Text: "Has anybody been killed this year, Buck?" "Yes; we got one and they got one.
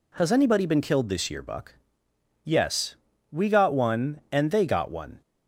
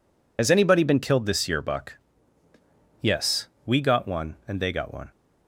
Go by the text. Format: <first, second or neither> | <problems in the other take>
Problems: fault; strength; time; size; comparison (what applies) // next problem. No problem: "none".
first | loses the start of "Has"; at 0.3 s; 45 ms